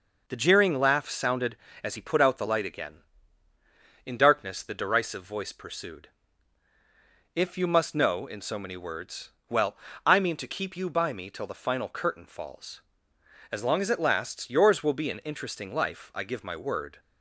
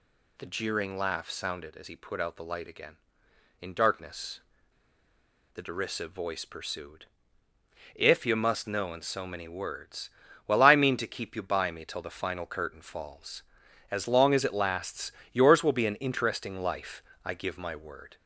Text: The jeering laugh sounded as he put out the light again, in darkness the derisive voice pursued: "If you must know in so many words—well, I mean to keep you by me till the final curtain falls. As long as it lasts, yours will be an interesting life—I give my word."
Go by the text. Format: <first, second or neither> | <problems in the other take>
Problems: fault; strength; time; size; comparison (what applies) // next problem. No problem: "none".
first | pauses between "darkness" and "the"; at 4.4 s; 1.1 s long